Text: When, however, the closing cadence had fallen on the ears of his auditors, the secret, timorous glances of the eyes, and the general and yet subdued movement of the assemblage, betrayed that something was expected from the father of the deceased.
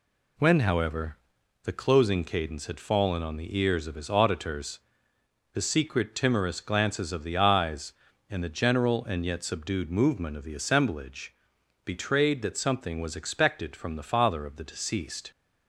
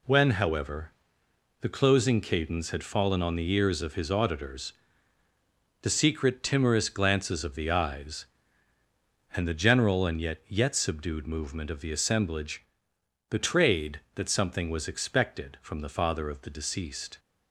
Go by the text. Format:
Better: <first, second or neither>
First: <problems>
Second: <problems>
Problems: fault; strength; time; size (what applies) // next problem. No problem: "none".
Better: first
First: none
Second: says "yet" twice; at 10.4 s